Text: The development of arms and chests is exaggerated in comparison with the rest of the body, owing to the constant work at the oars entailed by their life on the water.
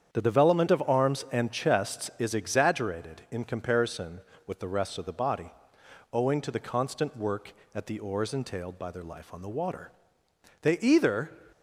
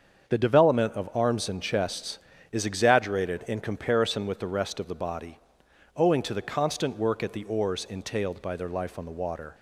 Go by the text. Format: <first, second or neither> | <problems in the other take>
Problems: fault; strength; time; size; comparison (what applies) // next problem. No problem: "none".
second | starts louder than the rest; strong; until 1.1 s; 8.5 dB; also in the second // goes on to say "They either"; noticeable; from 10.6 s on; 0.78 s long